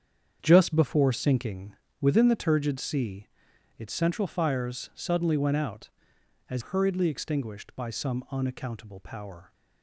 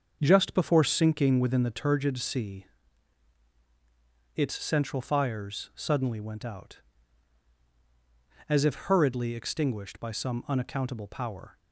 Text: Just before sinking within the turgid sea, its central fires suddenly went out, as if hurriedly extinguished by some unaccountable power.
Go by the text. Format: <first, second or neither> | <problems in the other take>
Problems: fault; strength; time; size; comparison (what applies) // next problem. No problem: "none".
second | starts louder than the rest; strong; until 1.4 s; 8 dB; also in the second // pauses between "sinking" and "within"; slight; at 1.7 s; 0.26 s long // skips "if"; at 6.6 s